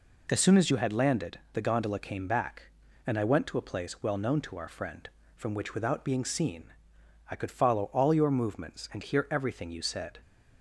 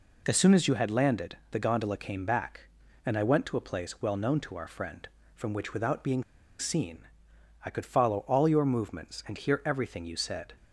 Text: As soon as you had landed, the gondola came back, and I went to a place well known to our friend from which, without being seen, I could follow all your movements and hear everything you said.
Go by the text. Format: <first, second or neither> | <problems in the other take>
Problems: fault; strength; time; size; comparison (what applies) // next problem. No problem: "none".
first | pauses between "being" and "seen"; slight; at 6.2 s; 0.35 s long